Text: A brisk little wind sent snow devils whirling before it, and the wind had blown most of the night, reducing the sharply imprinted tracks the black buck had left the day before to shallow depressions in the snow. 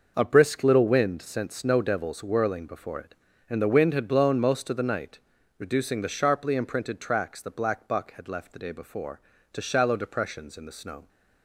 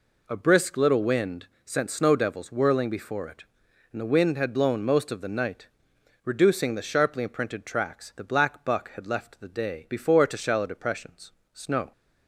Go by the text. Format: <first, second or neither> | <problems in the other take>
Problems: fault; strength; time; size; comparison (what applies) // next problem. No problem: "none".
first | pauses between "wind" and "sent"; slight; at 1.4 s; 0.20 s long // skips "in the"; at 11.4 s